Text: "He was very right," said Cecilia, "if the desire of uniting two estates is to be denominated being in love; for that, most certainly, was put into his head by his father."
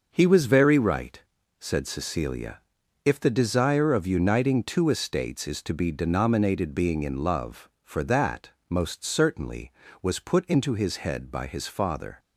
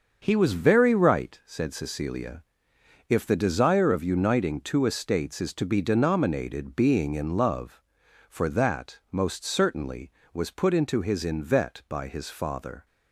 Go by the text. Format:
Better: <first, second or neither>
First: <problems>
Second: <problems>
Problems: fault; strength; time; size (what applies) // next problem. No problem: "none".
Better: first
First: none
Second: starts louder than the rest; until 1.2 s; 6.5 dB // says "invet" for "head"; at 11.2 s